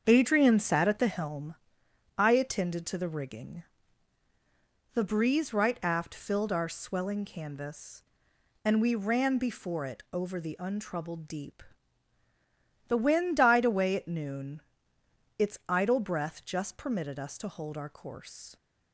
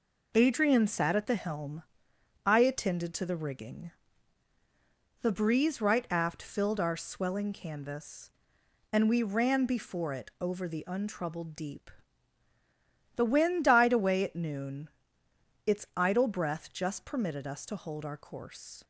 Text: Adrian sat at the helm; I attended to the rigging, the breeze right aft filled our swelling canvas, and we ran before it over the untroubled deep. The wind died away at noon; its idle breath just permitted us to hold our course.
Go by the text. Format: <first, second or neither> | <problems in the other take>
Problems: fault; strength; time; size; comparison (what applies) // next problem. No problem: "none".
second | starts louder than the rest; until 1.4 s; 7 dB